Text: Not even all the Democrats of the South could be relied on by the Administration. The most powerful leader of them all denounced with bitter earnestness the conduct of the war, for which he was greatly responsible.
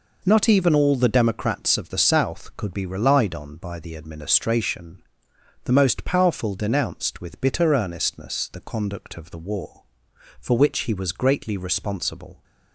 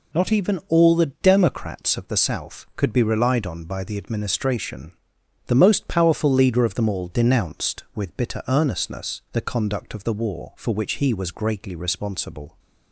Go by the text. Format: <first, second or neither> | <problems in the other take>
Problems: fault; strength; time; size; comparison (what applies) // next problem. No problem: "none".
second | skips "leader of them all"; at 6.5 s